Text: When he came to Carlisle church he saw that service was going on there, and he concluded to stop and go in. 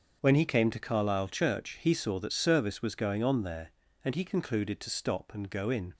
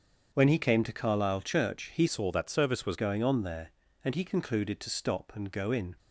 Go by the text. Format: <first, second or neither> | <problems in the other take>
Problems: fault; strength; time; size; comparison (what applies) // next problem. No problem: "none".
first | starts louder than the rest; strong; until 1.3 s; 7.5 dB; also in the first // changes voice from "saw" to "was"; from 2.0 to 2.9 s; 0.9 s long